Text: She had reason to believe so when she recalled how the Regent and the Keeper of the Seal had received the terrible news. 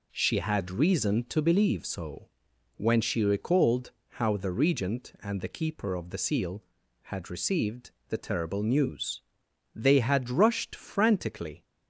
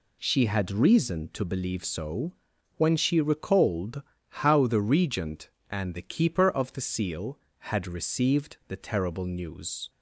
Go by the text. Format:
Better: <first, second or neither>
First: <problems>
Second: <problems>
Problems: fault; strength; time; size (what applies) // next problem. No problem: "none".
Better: second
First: pauses between "so" and "when"; noticeable; at 2.2 s; 0.48 s long // pauses between "recalled" and "how"; slight; at 3.9 s; 0.16 s long // pauses between "received" and "the"; slight; at 7.9 s; 0.16 s long // goes on to say "They had rushed frantically"; strong; from 9.7 s on; 1.8 s long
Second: pauses between "so" and "when"; at 2.3 s; 0.42 s long // pauses between "recalled" and "how"; slight; at 4.0 s; 0.26 s long